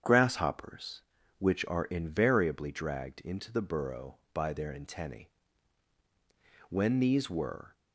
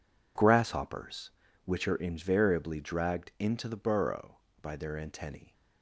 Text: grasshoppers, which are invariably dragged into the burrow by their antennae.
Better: second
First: starts louder than the rest; strong; until 1.4 s; 8 dB // goes on to say "When these were"; noticeable; from 6.6 s on; 1.0 s long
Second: none

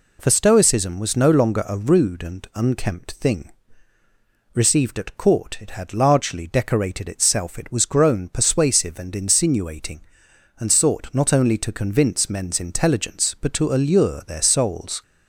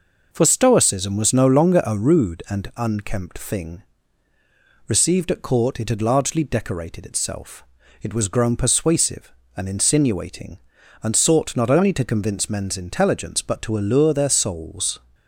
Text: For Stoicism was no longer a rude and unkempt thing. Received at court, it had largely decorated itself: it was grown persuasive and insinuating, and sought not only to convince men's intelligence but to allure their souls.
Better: neither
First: none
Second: none

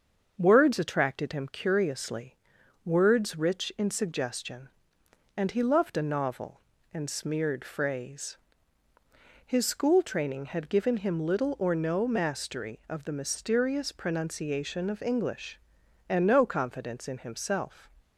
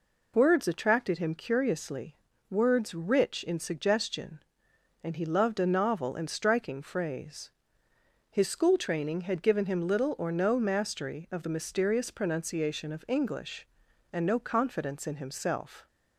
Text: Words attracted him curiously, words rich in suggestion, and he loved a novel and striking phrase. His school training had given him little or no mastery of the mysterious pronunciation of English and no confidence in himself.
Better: second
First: starts louder than the rest; until 1.3 s; 6.5 dB // says "smeared" for "striking"; at 7.0 s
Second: none

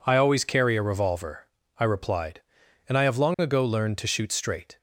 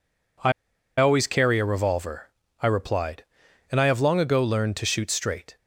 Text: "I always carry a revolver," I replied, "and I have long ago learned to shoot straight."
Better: first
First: none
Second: pauses between "I" and "always"; noticeable; at 0.5 s; 0.47 s long

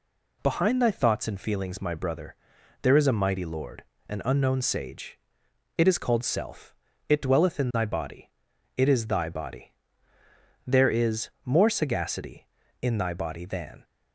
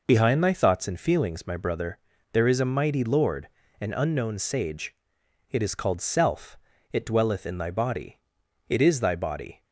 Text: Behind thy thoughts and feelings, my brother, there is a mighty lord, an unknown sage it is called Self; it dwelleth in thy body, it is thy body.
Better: second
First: pauses between "sage" and "it"; noticeable; at 5.1 s; 0.60 s long // goes on to say "There is more sagacity in thy body than"; strong; from 10.6 s on; 3.1 s long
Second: pauses between "sage" and "it"; noticeable; at 4.9 s; 0.56 s long

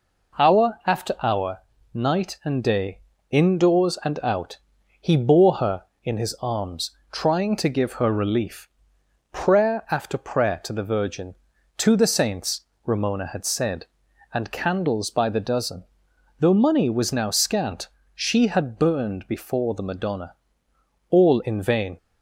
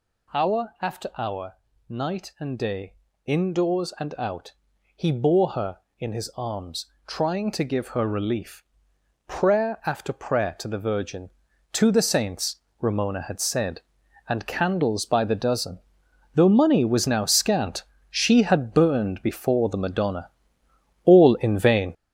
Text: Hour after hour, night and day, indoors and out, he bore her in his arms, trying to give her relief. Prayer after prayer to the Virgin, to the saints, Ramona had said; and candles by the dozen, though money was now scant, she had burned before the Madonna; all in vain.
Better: first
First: none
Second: gets louder; throughout; 7 dB

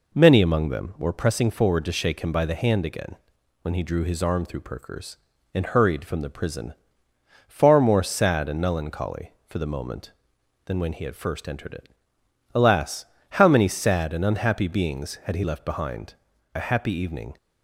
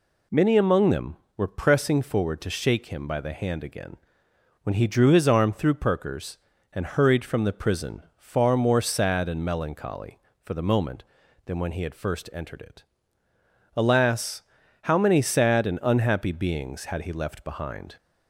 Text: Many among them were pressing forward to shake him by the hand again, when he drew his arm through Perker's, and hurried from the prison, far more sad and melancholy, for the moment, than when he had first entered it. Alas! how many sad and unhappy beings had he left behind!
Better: second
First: goes on to say "A happy evening"; noticeable; from 16.5 s on; 0.80 s long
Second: none

